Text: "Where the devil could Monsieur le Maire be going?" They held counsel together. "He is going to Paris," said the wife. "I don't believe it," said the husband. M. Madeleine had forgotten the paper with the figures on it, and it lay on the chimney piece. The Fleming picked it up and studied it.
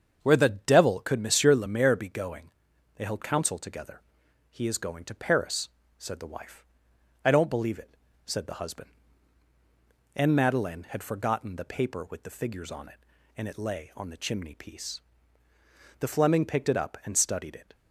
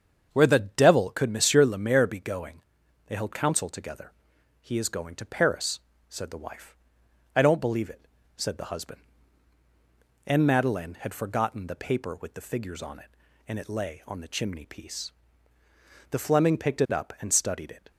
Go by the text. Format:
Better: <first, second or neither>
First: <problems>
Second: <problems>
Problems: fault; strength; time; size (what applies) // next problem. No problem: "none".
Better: neither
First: starts louder than the rest; strong; until 1.2 s; 7 dB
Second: starts louder than the rest; strong; until 1.3 s; 7 dB